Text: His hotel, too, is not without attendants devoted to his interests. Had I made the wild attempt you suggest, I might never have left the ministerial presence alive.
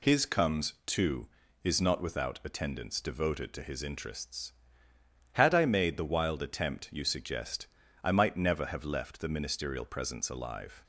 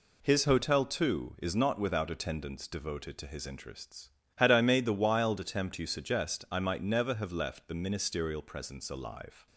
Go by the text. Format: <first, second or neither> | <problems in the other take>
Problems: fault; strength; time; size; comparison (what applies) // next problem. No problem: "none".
second | says "comes" for "hotel"; at 0.2 s